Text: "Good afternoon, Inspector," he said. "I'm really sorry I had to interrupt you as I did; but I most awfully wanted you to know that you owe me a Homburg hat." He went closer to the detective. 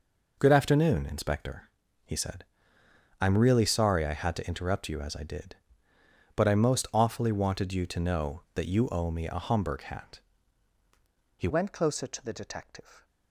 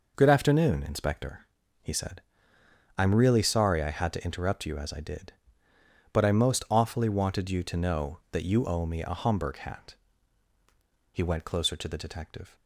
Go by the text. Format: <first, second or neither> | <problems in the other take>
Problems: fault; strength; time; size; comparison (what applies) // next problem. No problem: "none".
second | changes voice at "went"; from 11.4 s on; 1.6 s long